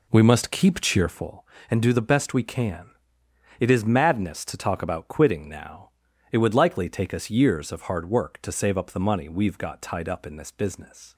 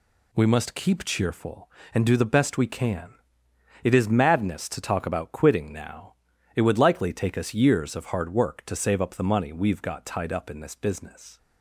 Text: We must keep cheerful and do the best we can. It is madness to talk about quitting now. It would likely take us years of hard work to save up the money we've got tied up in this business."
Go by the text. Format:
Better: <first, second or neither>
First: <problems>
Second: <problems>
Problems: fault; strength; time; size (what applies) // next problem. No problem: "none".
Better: second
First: starts louder than the rest; slight; until 1.4 s; 3.5 dB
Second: none